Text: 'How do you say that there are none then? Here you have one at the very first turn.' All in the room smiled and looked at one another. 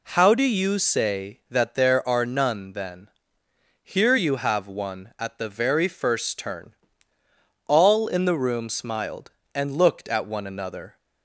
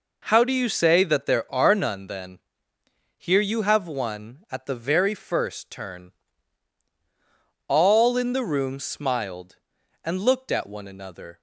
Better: neither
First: none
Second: none

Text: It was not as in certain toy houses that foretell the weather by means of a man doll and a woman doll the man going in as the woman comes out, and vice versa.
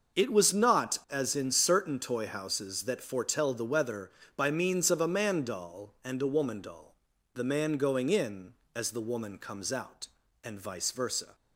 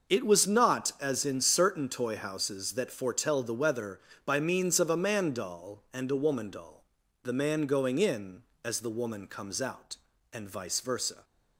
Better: neither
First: starts louder than the rest; noticeable; until 1.2 s; 6 dB // pauses between "doll" and "the"; at 6.9 s; 0.40 s long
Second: starts louder than the rest; noticeable; until 1.1 s; 6 dB // pauses between "doll" and "the"; at 6.8 s; 0.40 s long

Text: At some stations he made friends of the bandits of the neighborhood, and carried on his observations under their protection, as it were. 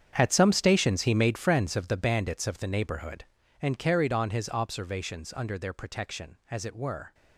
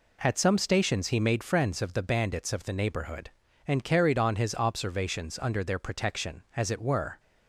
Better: second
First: gets quieter; strong; throughout; 15 dB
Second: none

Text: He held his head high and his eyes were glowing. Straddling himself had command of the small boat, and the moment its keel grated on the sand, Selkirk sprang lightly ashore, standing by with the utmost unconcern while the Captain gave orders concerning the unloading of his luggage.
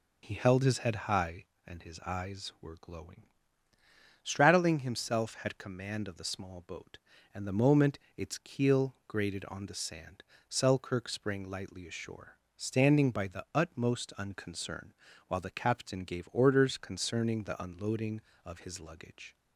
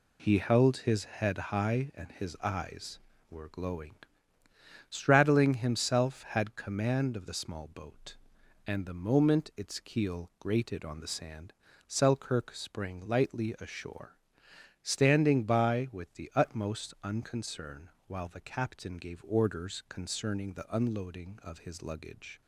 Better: second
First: pauses between "moment" and "its"; slight; at 7.9 s; 0.18 s long // skips "with"; at 13.2 s // pauses between "unconcern" and "while"; slight; at 14.9 s; 0.34 s long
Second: pauses between "unconcern" and "while"; slight; at 17.8 s; 0.18 s long

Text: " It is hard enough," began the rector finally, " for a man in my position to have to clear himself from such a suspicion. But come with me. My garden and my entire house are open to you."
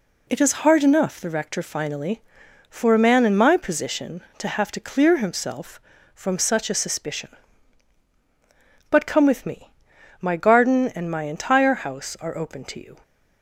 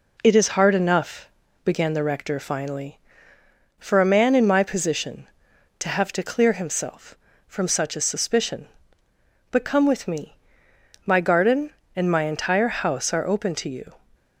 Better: second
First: skips "began"; at 1.2 s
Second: none

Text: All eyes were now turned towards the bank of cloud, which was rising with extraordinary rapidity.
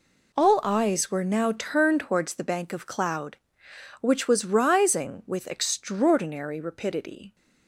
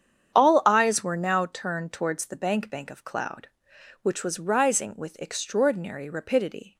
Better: first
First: none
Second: starts louder than the rest; strong; until 1.3 s; 8.5 dB // says "bank" twice; at 2.6 s

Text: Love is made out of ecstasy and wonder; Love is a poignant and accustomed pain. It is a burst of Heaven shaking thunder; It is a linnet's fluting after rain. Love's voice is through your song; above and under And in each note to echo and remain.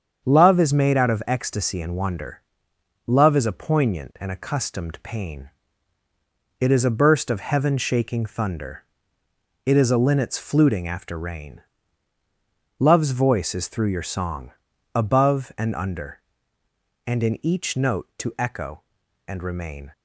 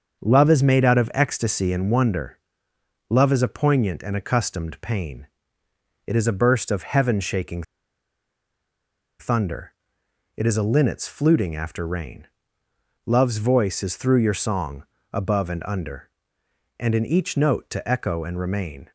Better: first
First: starts louder than the rest; strong; until 1.2 s; 7.5 dB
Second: starts louder than the rest; until 1.2 s; 7 dB // pauses between "shaking" and "thunder"; strong; at 7.6 s; 1.5 s long

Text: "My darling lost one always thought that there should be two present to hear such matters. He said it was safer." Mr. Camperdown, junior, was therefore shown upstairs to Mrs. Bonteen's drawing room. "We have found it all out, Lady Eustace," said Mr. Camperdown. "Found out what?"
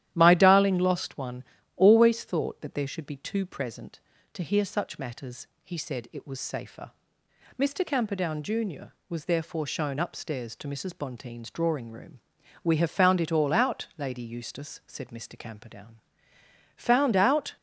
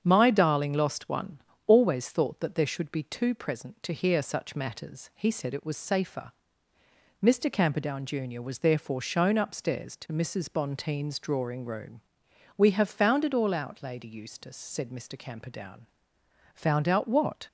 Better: second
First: starts louder than the rest; strong; until 1.1 s; 12 dB // pauses between "one" and "always"; slight; at 1.4 s; 0.32 s long // stops before "what"; at 17.5 s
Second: starts louder than the rest; strong; until 1.0 s; 8 dB // pauses between "one" and "always"; slight; at 1.4 s; 0.24 s long

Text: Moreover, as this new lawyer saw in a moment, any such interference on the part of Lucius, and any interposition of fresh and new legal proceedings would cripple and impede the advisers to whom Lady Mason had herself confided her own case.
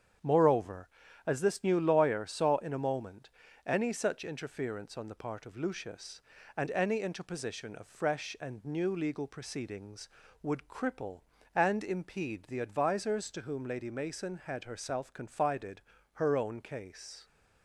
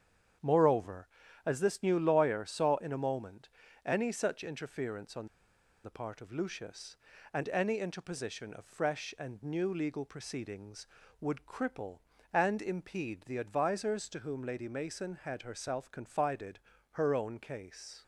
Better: first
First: starts louder than the rest; strong; until 1.5 s; 8 dB // pauses between "confided" and "her"; slight; at 15.8 s; 0.32 s long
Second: starts louder than the rest; strong; until 1.7 s; 8 dB // pauses between "on" and "the"; noticeable; at 5.2 s; 0.57 s long // pauses between "confided" and "her"; slight; at 16.5 s; 0.32 s long

